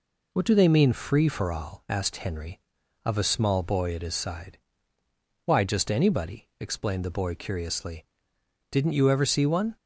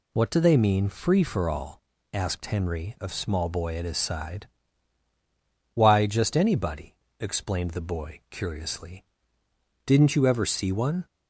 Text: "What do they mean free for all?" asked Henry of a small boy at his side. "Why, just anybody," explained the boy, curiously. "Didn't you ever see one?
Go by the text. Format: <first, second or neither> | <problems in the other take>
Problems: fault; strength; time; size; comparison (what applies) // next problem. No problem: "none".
first | skips "a"; at 3.1 s